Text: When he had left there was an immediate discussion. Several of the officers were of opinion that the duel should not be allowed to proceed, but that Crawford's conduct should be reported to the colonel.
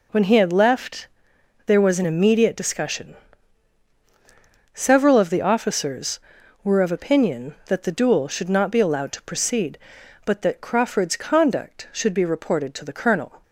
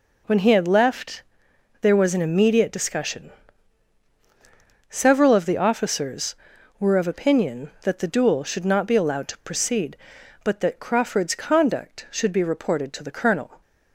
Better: neither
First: pauses between "left" and "there"; noticeable; at 1.0 s; 0.60 s long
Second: pauses between "left" and "there"; noticeable; at 1.2 s; 0.60 s long

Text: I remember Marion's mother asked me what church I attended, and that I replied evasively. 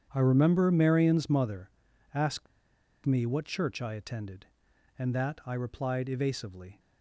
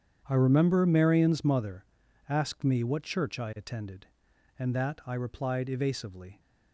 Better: second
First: starts louder than the rest; strong; until 1.1 s; 8.5 dB // pauses between "mother" and "asked"; at 1.6 s; 0.44 s long // pauses between "asked" and "me"; noticeable; at 2.4 s; 0.58 s long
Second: starts louder than the rest; strong; until 1.2 s; 8.5 dB // pauses between "mother" and "asked"; at 1.8 s; 0.44 s long

